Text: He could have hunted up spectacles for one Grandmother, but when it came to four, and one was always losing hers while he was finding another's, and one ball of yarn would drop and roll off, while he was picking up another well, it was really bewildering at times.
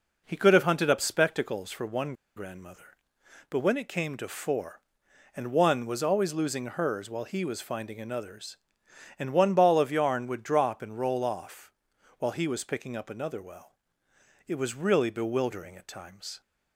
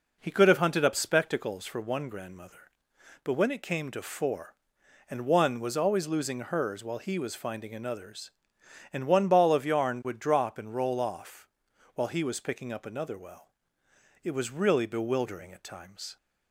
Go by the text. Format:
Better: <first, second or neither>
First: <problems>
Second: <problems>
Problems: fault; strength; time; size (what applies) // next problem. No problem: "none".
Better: second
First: pauses between "one" and "Grandmother"; slight; at 2.1 s; 0.22 s long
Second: none